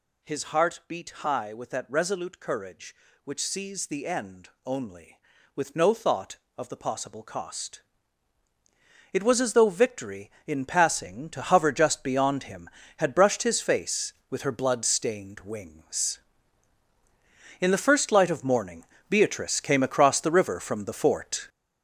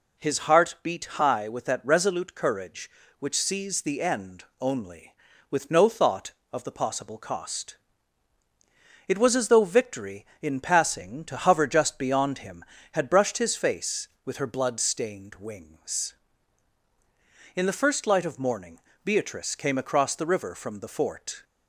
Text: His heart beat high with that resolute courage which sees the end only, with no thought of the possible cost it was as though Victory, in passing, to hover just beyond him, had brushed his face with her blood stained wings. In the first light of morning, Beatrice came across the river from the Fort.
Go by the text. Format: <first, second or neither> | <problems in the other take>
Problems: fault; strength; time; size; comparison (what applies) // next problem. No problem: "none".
second | gets louder; strong; throughout; 7.5 dB // pauses between "cost" and "it"; strong; at 7.8 s; 1.3 s long; strong in the second